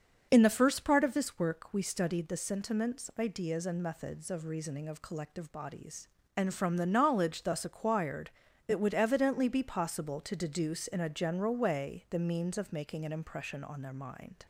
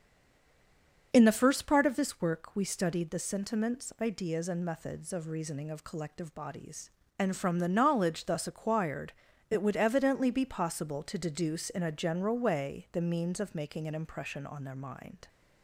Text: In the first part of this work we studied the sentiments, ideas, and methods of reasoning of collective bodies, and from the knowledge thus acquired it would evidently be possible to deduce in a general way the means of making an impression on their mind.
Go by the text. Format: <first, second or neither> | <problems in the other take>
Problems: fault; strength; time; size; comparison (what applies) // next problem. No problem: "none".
first | stays silent before the first word; until 1.1 s; 1.1 s long // starts louder than the rest; until 2.1 s; 6.5 dB; also in the first // pauses between "acquired" and "it"; at 9.1 s; 0.38 s long; also in the first